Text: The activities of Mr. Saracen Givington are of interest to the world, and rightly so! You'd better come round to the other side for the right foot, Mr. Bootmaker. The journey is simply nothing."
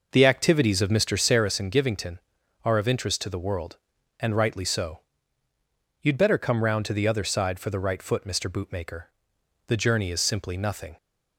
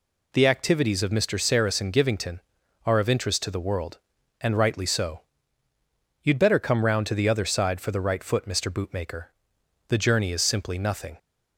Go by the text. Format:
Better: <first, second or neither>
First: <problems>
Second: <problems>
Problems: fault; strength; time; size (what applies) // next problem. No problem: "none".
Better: second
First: starts louder than the rest; noticeable; until 1.6 s; 5.5 dB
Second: none